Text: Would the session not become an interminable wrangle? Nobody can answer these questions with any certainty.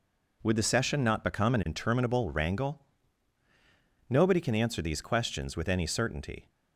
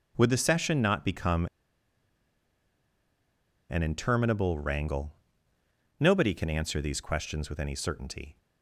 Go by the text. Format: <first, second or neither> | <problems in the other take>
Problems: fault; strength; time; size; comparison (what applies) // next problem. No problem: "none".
first | starts louder than the rest; strong; until 1.1 s; 8 dB // pauses between "become" and "an"; strong; at 1.4 s; 2.2 s long